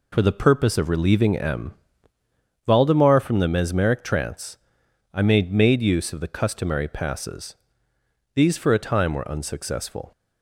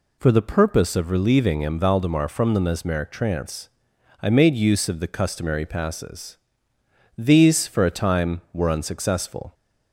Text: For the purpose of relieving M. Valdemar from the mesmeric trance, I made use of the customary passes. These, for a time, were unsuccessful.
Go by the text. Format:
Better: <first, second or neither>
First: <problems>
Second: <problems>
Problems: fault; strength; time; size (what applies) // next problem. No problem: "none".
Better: second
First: says "made" twice; at 5.5 s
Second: none